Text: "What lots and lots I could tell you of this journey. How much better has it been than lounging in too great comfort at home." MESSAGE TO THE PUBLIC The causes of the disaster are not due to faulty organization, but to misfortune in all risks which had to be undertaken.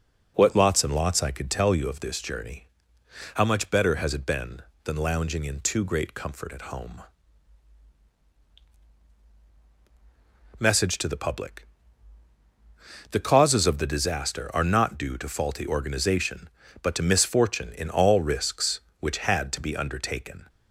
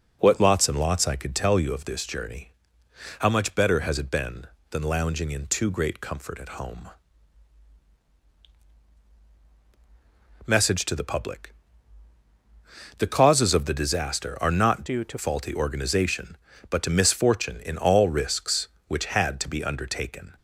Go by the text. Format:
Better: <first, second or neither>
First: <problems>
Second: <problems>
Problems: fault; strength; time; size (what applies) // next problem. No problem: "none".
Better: first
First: pauses between "PUBLIC" and "The"; strong; at 11.6 s; 1.4 s long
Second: pauses between "PUBLIC" and "The"; strong; at 11.5 s; 1.4 s long // changes voice from "due" to "to"; from 14.8 to 15.1 s; 0.3 s long